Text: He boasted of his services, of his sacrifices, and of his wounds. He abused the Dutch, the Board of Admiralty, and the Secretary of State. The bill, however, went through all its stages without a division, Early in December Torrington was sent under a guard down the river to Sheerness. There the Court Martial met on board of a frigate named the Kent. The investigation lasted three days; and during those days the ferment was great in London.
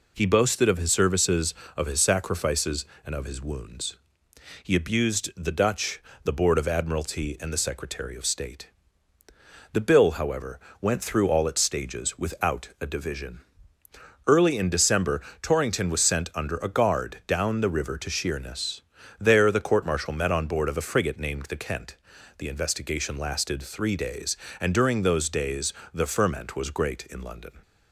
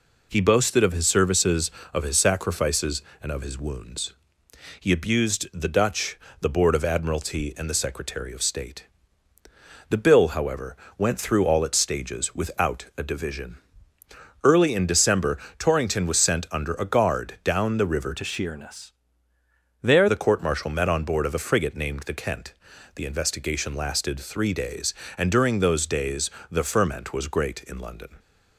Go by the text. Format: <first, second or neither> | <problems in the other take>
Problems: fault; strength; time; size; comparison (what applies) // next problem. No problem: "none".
first | pauses between "December" and "Torrington"; slight; at 15.3 s; 0.22 s long; slight in the first // changes voice from "to" to "There"; from 18.1 to 20.0 s; 1.9 s long // pauses between "days" and "the"; slight; at 26.3 s; 0.18 s long; slight in the first